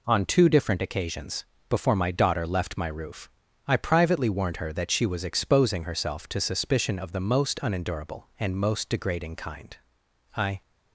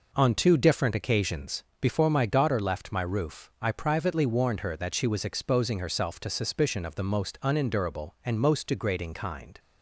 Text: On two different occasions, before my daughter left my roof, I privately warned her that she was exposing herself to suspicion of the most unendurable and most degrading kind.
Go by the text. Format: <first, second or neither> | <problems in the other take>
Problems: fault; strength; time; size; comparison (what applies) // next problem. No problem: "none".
second | goes on to say "I"; slight; from 10.3 s on; 0.24 s long